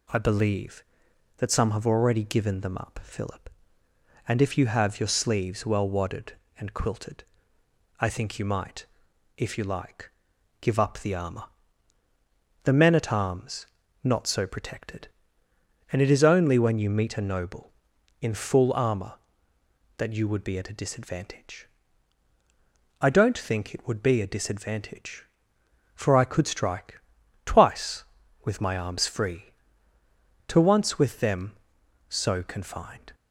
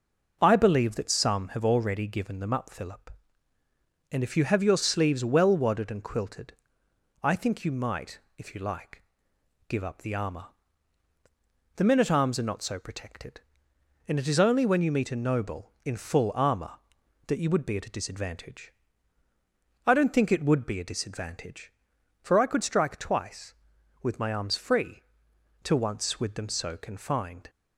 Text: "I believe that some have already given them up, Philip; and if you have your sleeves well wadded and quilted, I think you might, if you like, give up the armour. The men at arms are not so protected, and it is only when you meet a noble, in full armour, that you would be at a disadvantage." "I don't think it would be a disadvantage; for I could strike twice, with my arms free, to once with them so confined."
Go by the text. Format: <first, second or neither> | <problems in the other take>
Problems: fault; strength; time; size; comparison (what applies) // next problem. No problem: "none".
second | skips "are"; at 13.8 s // pauses between "strike" and "twice"; at 27.0 s; 0.44 s long